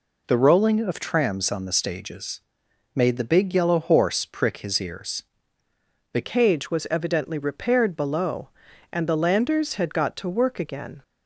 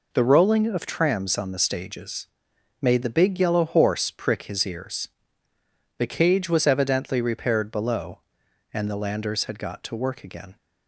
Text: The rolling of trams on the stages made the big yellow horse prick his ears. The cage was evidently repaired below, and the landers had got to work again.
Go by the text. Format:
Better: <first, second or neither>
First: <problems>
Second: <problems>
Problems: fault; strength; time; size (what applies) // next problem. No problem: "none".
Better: second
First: pauses between "stages" and "made"; noticeable; at 2.4 s; 0.54 s long // changes voice at "cage"; from 6.2 s on; 4.8 s long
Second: pauses between "stages" and "made"; noticeable; at 2.2 s; 0.54 s long